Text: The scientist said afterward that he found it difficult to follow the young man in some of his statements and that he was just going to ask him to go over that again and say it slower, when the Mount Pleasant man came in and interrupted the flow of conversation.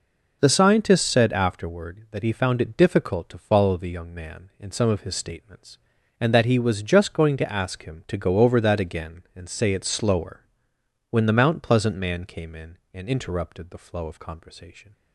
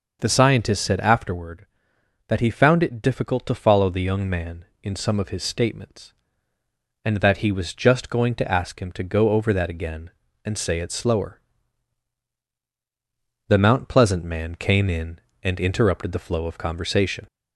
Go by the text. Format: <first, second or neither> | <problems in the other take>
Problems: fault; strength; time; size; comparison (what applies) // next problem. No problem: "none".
first | skips "when"; at 12.4 s